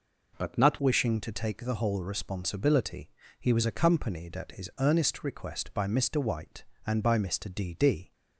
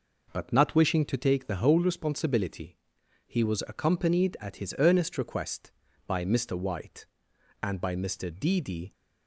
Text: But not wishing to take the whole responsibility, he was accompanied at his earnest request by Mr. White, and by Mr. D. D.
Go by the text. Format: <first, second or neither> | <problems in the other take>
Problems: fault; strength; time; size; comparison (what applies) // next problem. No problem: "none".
second | changes voice at "wishing"; from 0.8 s on; 7.3 s long